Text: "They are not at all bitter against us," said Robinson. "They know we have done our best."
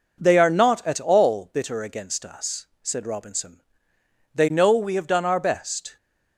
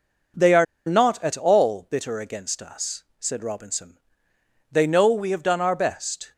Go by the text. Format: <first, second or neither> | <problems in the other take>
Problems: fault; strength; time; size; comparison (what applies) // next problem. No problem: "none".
first | pauses between "are" and "not"; slight; at 0.6 s; 0.21 s long